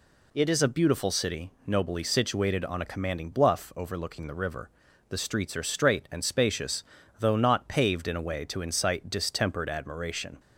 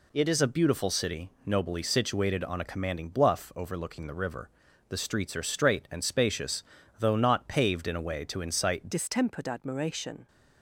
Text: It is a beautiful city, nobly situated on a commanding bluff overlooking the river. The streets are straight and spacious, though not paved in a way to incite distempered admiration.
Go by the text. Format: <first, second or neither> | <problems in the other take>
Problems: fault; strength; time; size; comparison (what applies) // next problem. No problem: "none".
first | changes voice at "distempered"; from 8.9 s on; 1.3 s long